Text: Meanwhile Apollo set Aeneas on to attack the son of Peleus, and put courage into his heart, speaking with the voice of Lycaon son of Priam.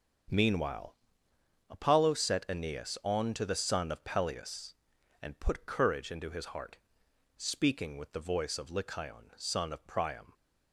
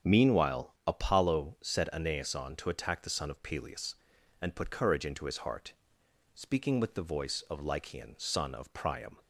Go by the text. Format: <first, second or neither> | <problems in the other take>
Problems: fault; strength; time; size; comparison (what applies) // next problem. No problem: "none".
second | starts louder than the rest; until 2.0 s; 6.5 dB; also in the second // pauses between "Meanwhile" and "Apollo"; noticeable; at 0.9 s; 0.76 s long // skips "attack"; at 3.4 s